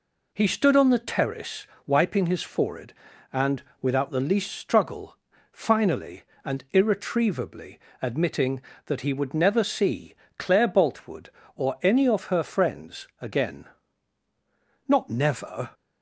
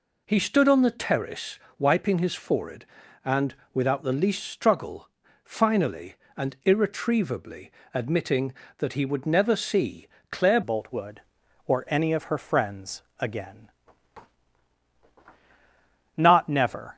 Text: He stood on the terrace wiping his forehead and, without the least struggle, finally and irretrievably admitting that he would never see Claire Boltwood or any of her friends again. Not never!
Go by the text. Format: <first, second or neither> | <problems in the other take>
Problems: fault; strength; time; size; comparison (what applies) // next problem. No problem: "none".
first | pauses between "terrace" and "wiping"; slight; at 1.5 s; 0.20 s long; slight in the first // pauses between "irretrievably" and "admitting"; slight; at 7.7 s; 0.22 s long; slight in the first // pauses between "see" and "Claire"; slight; at 10.0 s; 0.24 s long; slight in the first // changes voice at "Boltwood"; from 10.6 s on; 6.3 s long // pauses between "friends" and "again"; slight; at 13.0 s; 0.16 s long